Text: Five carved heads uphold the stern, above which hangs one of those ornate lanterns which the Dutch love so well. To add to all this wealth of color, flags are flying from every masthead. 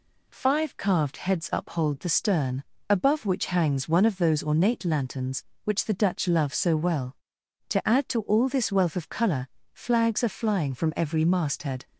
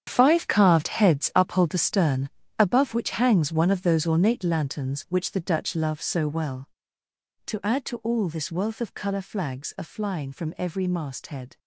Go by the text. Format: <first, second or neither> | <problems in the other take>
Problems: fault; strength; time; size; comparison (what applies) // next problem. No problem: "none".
first | gets quieter; strong; throughout; 12.5 dB